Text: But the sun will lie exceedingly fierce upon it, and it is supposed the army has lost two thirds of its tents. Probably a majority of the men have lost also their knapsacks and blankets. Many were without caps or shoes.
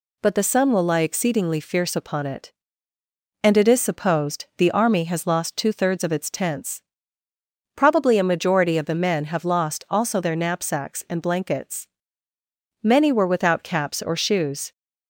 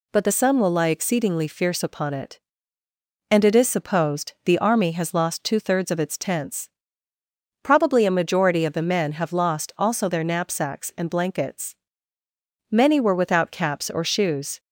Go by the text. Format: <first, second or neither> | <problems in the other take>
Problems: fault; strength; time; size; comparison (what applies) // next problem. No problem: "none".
neither | none